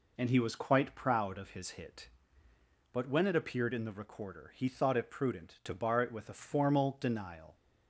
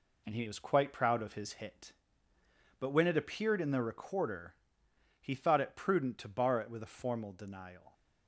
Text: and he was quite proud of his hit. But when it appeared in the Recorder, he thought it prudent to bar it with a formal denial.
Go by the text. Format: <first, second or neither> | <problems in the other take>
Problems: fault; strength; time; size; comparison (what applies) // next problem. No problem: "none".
first | gets quieter; noticeable; throughout; 5.5 dB